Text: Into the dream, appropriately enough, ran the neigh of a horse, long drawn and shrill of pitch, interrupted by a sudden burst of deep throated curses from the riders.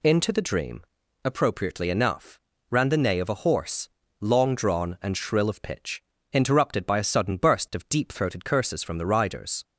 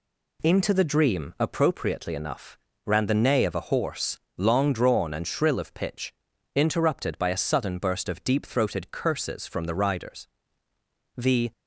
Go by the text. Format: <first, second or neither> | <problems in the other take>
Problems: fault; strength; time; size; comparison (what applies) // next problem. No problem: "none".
first | goes on to say "The"; slight; from 11.1 s on; 0.36 s long